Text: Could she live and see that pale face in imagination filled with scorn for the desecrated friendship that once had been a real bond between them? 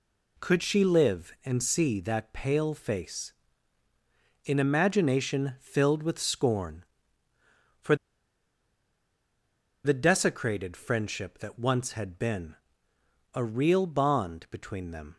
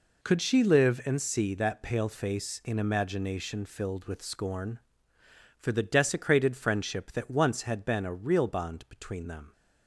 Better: second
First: pauses between "for" and "the"; strong; at 7.9 s; 1.8 s long // pauses between "been" and "a"; noticeable; at 12.5 s; 0.78 s long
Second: none

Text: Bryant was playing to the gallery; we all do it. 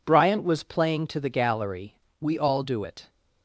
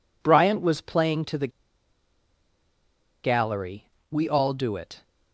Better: first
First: none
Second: pauses between "the" and "gallery"; strong; at 1.4 s; 1.7 s long

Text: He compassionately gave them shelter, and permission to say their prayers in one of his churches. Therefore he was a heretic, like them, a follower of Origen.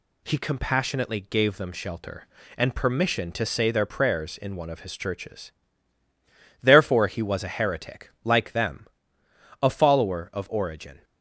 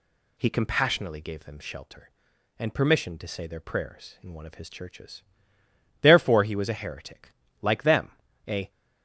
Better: first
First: none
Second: stops before "follower of Origen"; at 8.6 s

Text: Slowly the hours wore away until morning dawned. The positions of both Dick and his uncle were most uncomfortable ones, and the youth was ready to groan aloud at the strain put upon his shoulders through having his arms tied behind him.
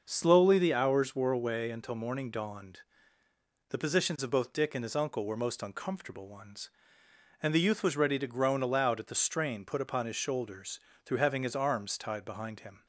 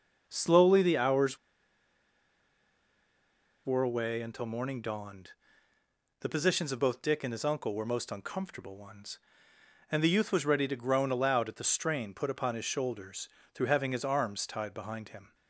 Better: first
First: starts louder than the rest; noticeable; until 1.0 s; 6 dB // pauses between "shoulders" and "through"; slight; at 10.7 s; 0.26 s long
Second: starts louder than the rest; noticeable; until 1.2 s; 6 dB // pauses between "hours" and "wore"; strong; at 1.3 s; 2.2 s long // pauses between "shoulders" and "through"; slight; at 13.2 s; 0.26 s long

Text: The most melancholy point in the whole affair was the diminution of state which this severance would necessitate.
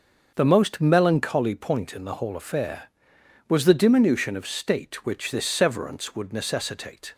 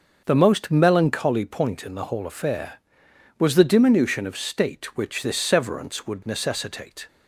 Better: neither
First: starts louder than the rest; noticeable; until 1.3 s; 6 dB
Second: starts louder than the rest; noticeable; until 1.2 s; 6 dB

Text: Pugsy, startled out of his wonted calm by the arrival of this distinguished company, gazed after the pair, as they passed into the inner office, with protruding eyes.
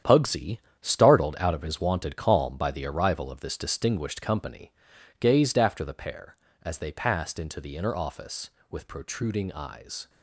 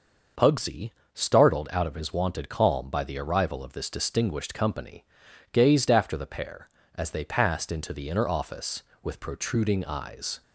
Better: second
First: gets quieter; strong; throughout; 9.5 dB // starts louder than the rest; strong; until 1.2 s; 9.5 dB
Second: starts louder than the rest; noticeable; until 1.6 s; 6 dB

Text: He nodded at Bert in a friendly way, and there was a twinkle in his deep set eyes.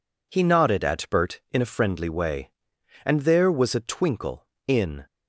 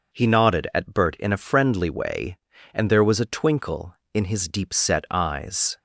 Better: second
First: stops before "his deep set eyes"; at 5.0 s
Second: none

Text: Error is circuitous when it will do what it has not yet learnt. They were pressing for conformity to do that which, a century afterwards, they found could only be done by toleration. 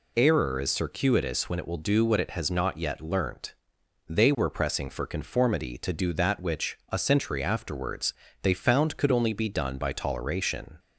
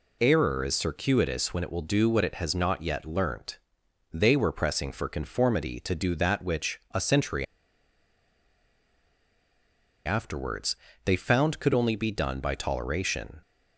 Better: first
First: none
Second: pauses between "century" and "afterwards"; strong; at 7.4 s; 2.6 s long

